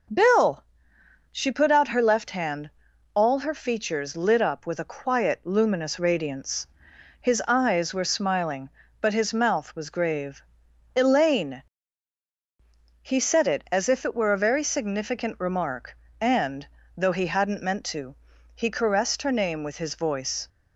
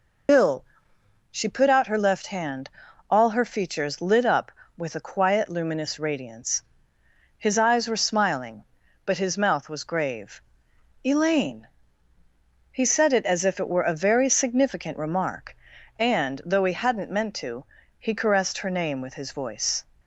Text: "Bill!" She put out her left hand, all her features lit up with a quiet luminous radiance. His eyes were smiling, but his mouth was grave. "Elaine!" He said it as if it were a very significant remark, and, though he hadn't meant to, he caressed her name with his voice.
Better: first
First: none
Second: loses the start of "Bill"; at 0.2 s; 70 ms

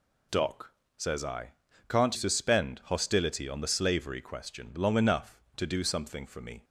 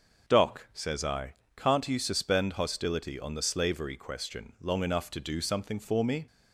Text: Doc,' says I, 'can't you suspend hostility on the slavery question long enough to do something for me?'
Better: second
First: skips "you"; at 2.1 s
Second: none

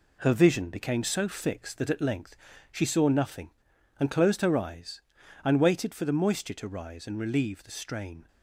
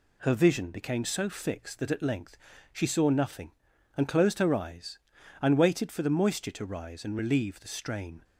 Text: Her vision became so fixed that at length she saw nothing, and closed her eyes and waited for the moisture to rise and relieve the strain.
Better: second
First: gets quieter; noticeable; throughout; 6 dB // pauses between "length" and "she"; slight; at 2.3 s; 0.36 s long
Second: pauses between "length" and "she"; slight; at 2.3 s; 0.36 s long

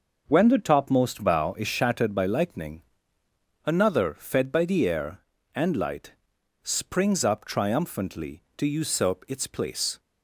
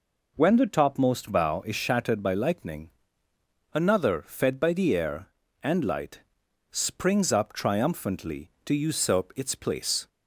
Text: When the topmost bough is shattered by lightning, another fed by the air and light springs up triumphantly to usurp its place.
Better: second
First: gets quieter; strong; throughout; 7.5 dB // pauses between "light" and "springs"; noticeable; at 6.1 s; 0.50 s long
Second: pauses between "light" and "springs"; noticeable; at 6.2 s; 0.50 s long

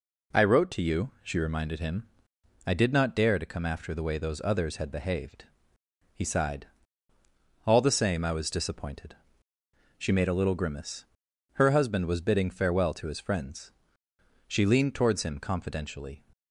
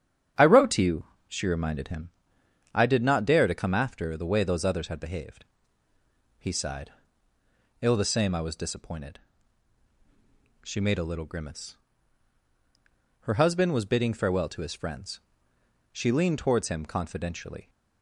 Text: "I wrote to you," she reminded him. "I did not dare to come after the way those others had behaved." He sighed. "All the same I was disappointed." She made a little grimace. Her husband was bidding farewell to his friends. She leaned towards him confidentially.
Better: first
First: none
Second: starts louder than the rest; strong; until 1.6 s; 9 dB // says "Ill" for "All"; at 7.8 s

